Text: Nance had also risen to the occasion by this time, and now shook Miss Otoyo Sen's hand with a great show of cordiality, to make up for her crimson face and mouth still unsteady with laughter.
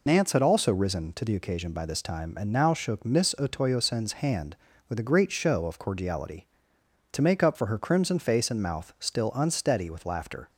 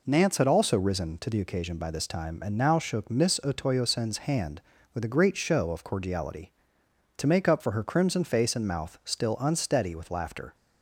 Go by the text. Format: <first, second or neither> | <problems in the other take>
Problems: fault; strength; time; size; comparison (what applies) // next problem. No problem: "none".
second | loses the start of "Nance"; at 0.0 s; 65 ms